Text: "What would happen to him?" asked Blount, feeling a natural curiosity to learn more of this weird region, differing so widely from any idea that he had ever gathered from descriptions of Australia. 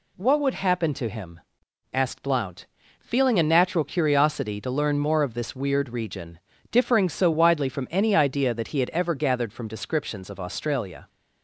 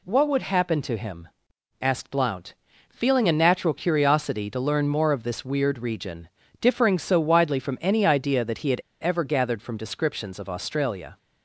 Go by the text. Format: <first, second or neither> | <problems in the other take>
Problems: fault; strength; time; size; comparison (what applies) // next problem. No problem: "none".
first | pauses between "had" and "ever"; slight; at 8.8 s; 0.20 s long